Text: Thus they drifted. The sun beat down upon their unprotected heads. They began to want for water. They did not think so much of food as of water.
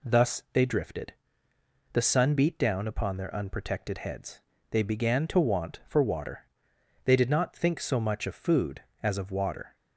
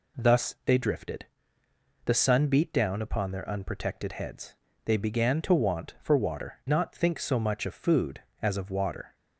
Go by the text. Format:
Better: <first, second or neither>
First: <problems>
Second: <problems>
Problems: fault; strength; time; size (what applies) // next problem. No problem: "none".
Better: first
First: none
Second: skips "They did"; at 6.6 s